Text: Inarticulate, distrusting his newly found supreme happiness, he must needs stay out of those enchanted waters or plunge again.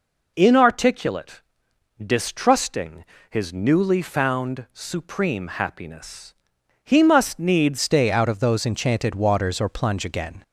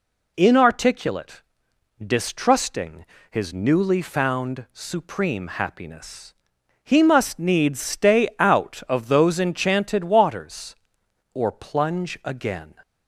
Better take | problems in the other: second | pauses between "distrusting" and "his"; slight; at 3.0 s; 0.26 s long; slight in the second // changes voice at "stay"; from 7.8 s on; 2.6 s long

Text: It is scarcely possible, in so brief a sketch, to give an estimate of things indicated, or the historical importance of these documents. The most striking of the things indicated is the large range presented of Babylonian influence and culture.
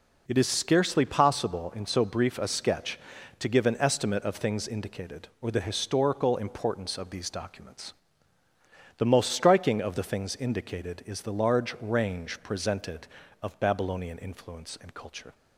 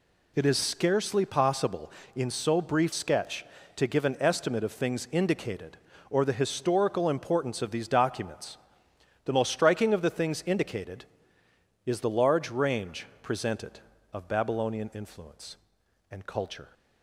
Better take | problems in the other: first | skips "a"; at 2.9 s // pauses between "range" and "presented"; slight; at 13.0 s; 0.16 s long

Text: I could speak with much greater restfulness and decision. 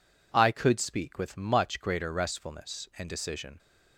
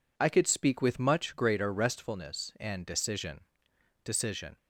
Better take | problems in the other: first | says "decision" twice; at 4.0 s

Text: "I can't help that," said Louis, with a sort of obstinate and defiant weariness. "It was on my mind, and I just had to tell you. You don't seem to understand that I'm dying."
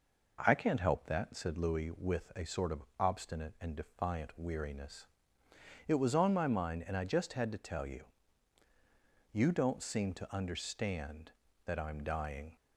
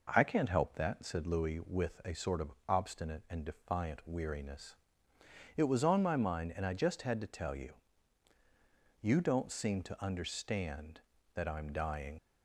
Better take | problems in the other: first | leaves "dying" unfinished; at 12.1 s; 55 ms

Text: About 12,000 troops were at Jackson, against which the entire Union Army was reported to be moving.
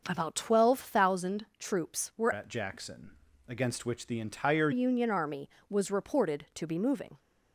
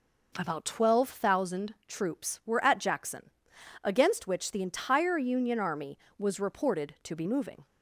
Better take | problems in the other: second | starts louder than the rest; until 1.0 s; 6.5 dB // changes voice from "at" to "entire"; from 2.3 to 4.7 s; 2.4 s long

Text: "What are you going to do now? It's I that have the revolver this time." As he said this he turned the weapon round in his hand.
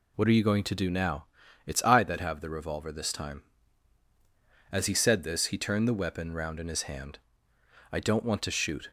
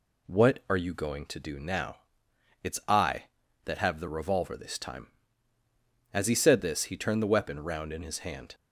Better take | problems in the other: second | goes on to say "I don't want to shoot"; noticeable; from 7.9 s on; 1.0 s long

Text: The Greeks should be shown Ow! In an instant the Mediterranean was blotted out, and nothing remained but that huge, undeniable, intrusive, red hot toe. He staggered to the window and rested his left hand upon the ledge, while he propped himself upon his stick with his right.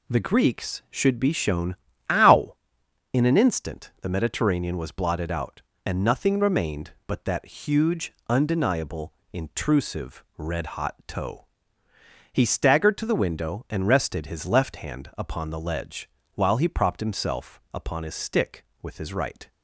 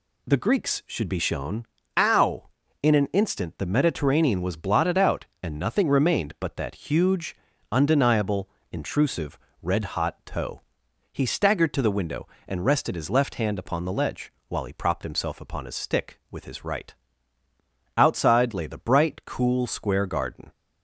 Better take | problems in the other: first | pauses between "shown" and "Ow"; slight; at 1.6 s; 0.32 s long; slight in the first // goes on to say "Outside lay the bright cool square garden"; strong; from 17.9 s on; 2.5 s long

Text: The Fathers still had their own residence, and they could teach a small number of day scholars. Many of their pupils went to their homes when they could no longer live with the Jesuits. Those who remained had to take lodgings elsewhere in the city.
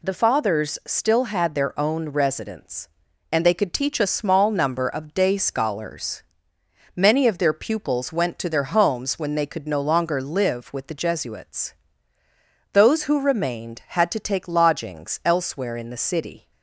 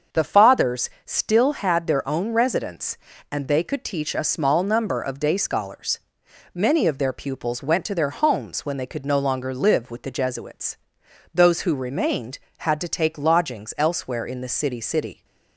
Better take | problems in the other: first | starts louder than the rest; until 1.3 s; 6.5 dB // pauses between "Fathers" and "still"; slight; at 0.8 s; 0.16 s long // says "city" twice; at 14.7 s

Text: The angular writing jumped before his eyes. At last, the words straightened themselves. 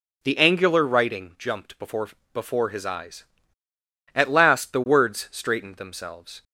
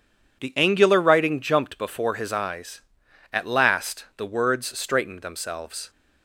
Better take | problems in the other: second | says "before" twice; at 2.3 s

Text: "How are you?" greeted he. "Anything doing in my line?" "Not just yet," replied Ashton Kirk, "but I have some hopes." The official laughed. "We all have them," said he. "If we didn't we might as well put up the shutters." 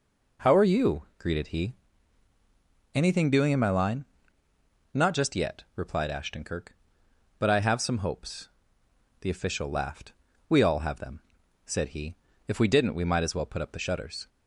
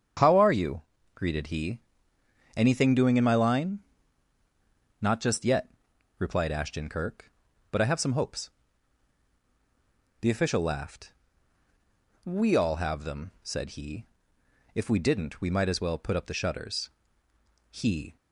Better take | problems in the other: first | starts louder than the rest; strong; until 1.5 s; 7.5 dB // goes on to say "He"; slight; from 17.6 s on; 0.46 s long

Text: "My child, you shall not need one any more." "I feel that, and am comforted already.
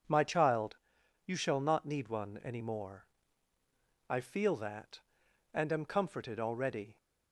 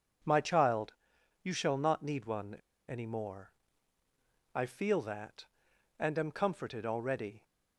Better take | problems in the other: first | pauses between "one" and "any"; slight; at 2.5 s; 0.34 s long

